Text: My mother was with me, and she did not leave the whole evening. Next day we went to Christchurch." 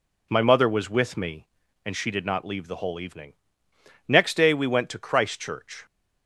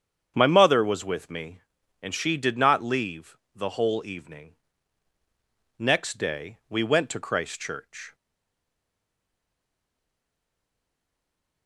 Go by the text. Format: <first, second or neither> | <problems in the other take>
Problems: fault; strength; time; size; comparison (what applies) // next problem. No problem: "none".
first | starts louder than the rest; strong; until 1.3 s; 8 dB // pauses between "leave" and "the"; slight; at 3.3 s; 0.18 s long // stays silent after the last word; strong; from 8.1 s on; 3.5 s long